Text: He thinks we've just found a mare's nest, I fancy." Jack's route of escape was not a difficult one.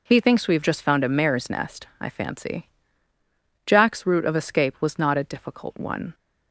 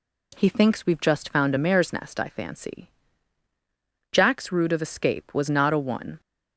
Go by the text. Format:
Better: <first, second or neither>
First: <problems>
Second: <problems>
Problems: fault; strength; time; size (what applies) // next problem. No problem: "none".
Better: first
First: none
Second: skips "difficult"; at 5.7 s